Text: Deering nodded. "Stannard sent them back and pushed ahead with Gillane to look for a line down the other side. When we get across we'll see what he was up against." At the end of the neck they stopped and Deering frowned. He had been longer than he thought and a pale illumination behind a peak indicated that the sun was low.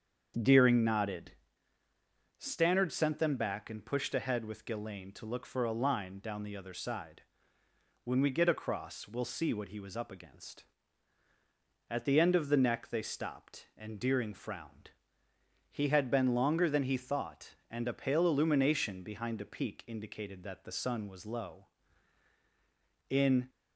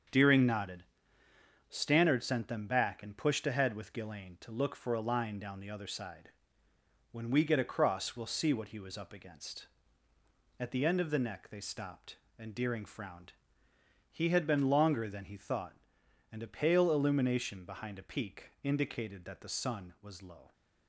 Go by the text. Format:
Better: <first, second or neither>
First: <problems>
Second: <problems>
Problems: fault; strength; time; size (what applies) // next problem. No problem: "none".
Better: second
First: starts louder than the rest; until 2.4 s; 7 dB // goes on to say "In"; slight; from 23.0 s on; 0.40 s long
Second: starts louder than the rest; until 1.9 s; 7 dB